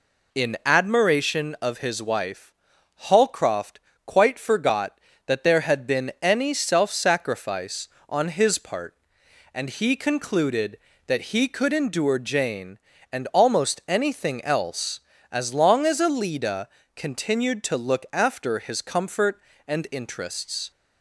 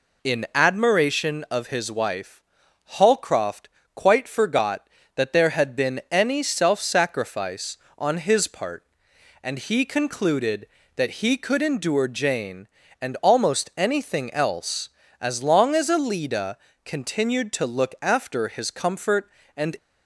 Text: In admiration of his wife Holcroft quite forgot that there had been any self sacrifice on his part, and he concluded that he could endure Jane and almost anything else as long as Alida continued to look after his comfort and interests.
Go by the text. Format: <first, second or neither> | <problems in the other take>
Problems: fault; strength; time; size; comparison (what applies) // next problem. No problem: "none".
first | pauses between "wife" and "Holcroft"; noticeable; at 2.4 s; 0.54 s long; noticeable in the first // pauses between "Holcroft" and "quite"; slight; at 3.6 s; 0.24 s long; slight in the first // pauses between "Alida" and "continued"; slight; at 16.5 s; 0.26 s long; slight in the first // stops before "interests"; at 19.7 s